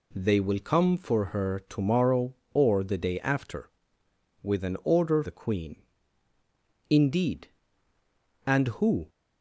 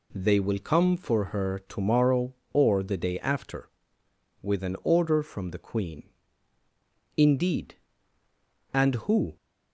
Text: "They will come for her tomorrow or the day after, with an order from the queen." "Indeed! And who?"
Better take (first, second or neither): second